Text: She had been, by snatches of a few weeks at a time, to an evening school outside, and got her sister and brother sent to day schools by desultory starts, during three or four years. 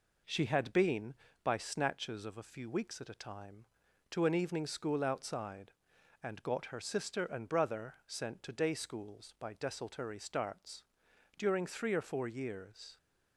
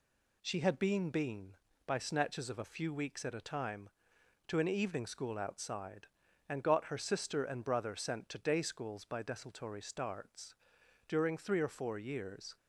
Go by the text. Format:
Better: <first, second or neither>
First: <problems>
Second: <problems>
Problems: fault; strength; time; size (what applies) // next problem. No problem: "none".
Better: first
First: none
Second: says "been" twice; at 1.0 s